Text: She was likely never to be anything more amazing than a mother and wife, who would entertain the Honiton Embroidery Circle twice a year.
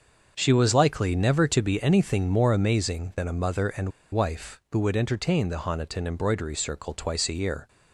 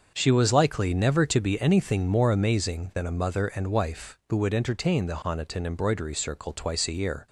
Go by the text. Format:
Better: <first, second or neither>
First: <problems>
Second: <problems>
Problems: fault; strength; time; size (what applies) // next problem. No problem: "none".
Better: second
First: starts louder than the rest; until 1.3 s; 6.5 dB // pauses between "and" and "wife"; slight; at 3.9 s; 0.22 s long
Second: starts louder than the rest; until 1.1 s; 6.5 dB